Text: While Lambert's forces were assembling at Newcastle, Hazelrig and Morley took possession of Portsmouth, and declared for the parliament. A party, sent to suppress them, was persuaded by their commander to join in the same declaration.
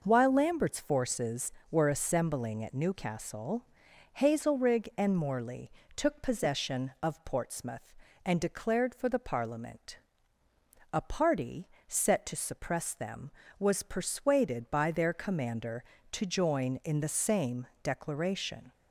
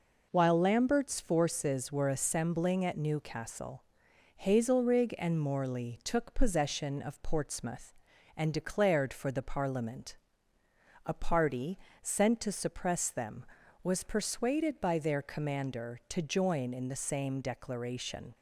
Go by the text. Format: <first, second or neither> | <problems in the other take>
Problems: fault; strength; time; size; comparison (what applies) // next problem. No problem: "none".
second | pauses between "Morley" and "took"; slight; at 5.7 s; 0.24 s long // says "set" for "sent"; at 11.8 s // pauses between "same" and "declaration"; slight; at 17.6 s; 0.16 s long